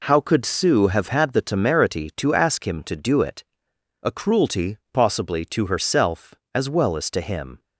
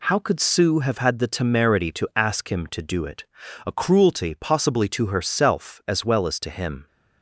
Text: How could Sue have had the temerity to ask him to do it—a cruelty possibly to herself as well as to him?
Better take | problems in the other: neither | none

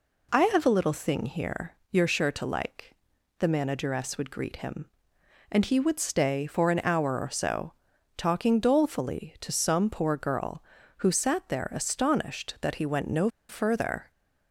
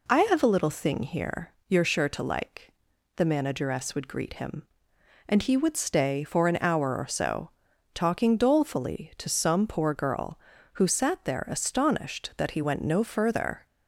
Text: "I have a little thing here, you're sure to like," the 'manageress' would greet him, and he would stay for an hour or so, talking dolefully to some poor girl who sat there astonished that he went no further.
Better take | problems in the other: second | pauses between "no" and "further"; slight; at 13.2 s; 0.21 s long

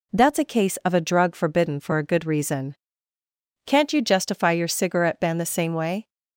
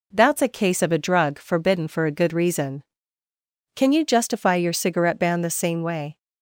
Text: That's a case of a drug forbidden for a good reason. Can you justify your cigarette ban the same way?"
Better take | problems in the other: second | says "Can't" for "Can"; at 3.6 s

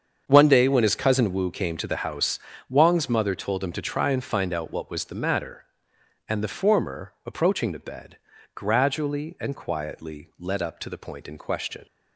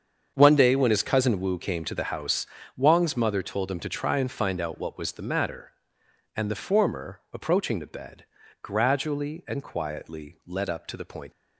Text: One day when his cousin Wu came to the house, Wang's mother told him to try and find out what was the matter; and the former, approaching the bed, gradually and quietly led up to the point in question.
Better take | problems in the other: first | starts louder than the rest; strong; until 1.3 s; 7 dB; strong in the first // stops before "in question"; at 11.3 s

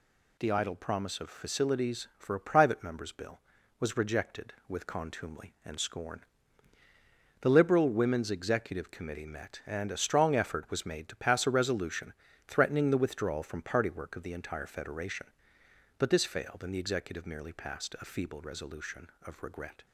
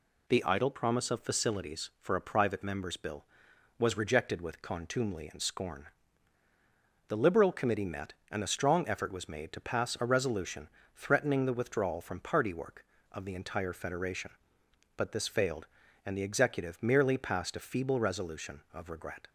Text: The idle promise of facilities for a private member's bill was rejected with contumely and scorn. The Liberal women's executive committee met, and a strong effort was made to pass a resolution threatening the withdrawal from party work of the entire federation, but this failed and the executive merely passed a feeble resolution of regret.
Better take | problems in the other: first | skips "women's executive"; at 7.5 s // pauses between "resolution" and "threatening"; slight; at 10.6 s; 0.28 s long; slight in the first

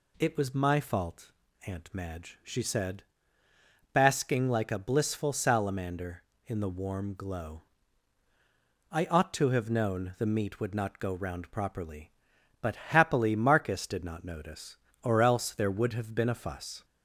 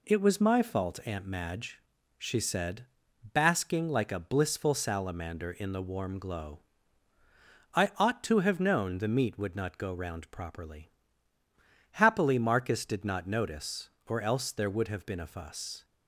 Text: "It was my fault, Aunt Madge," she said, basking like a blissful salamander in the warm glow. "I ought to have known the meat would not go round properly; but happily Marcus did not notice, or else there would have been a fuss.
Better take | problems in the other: first | skips "but"; at 11.4 s

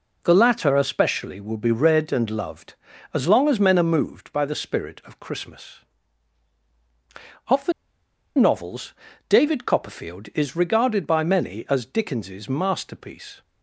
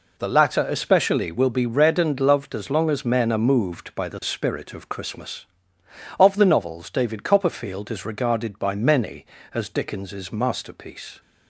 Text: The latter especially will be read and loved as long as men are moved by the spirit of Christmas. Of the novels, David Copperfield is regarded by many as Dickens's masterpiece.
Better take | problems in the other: second | pauses between "the" and "novels"; noticeable; at 7.7 s; 0.64 s long

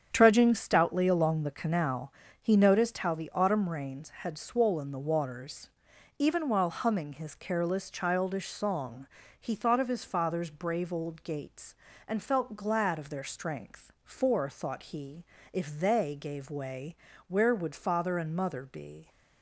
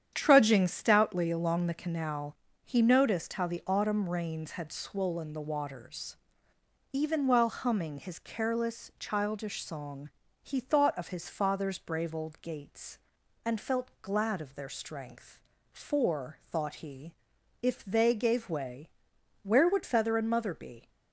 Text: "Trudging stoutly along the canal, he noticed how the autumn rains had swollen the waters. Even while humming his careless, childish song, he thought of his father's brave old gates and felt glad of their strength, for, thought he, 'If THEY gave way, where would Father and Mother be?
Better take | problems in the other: first | starts louder than the rest; strong; until 1.1 s; 9 dB; strong in the first // says "Feather" for "Father"; at 19.8 s

